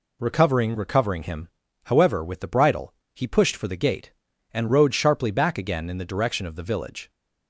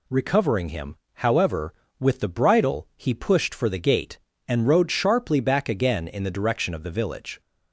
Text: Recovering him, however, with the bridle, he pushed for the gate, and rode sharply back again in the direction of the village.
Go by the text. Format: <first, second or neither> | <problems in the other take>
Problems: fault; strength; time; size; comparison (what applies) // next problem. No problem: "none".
second | says "Recovering" twice; at 0.7 s